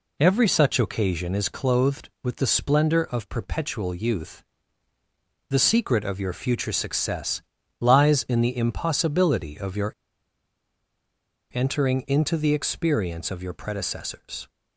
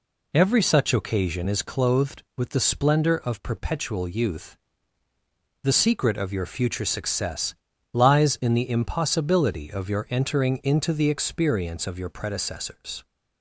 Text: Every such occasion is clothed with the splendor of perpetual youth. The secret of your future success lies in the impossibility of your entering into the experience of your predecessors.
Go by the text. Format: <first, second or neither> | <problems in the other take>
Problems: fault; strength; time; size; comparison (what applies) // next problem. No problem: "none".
second | pauses between "success" and "lies"; at 7.4 s; 0.38 s long; also in the second // pauses between "your" and "entering"; strong; at 9.9 s; 1.6 s long